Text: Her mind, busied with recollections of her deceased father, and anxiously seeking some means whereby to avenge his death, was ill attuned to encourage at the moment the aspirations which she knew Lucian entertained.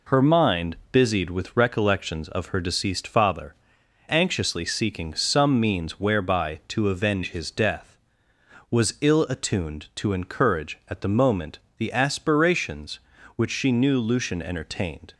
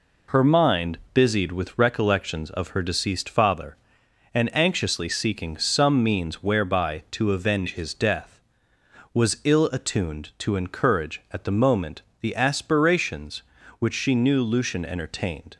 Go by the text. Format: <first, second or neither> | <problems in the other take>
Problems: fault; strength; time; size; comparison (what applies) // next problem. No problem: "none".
second | skips "and"; at 3.8 s // pauses between "moment" and "the"; slight; at 11.5 s; 0.18 s long; slight in the second